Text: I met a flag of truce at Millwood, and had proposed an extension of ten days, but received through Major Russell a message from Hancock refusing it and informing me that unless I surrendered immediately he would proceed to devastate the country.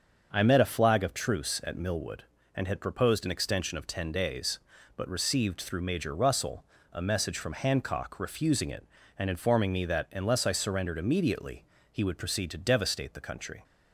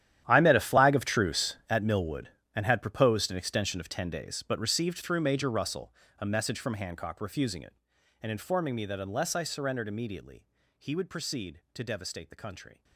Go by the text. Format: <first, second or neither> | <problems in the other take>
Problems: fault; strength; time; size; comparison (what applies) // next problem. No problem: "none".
first | gets quieter; strong; throughout; 17 dB // starts louder than the rest; strong; until 1.2 s; 11 dB; also in the first // pauses between "Russell" and "a"; slight; at 5.9 s; 0.24 s long; slight in the first // pauses between "immediately" and "he"; slight; at 10.4 s; 0.32 s long; slight in the first